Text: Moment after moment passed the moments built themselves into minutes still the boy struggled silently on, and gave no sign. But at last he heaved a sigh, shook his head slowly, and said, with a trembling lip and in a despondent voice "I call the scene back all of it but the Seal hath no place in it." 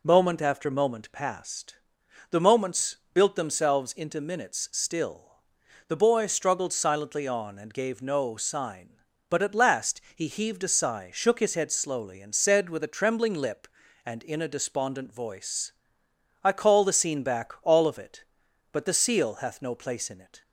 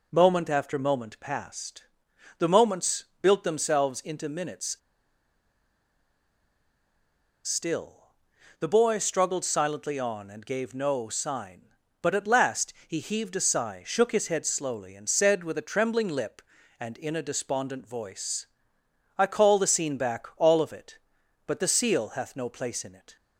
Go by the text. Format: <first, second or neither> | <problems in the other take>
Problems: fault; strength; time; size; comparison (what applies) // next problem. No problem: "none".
first | pauses between "passed" and "the"; noticeable; at 1.8 s; 0.56 s long; noticeable in the first // pauses between "moments" and "built"; slight; at 3.0 s; 0.16 s long; slight in the first // pauses between "minutes" and "still"; strong; at 4.7 s; 2.6 s long // pauses between "still" and "the"; noticeable; at 8.1 s; 0.46 s long; noticeable in the first // pauses between "voice" and "I"; noticeable; at 18.4 s; 0.72 s long; noticeable in the first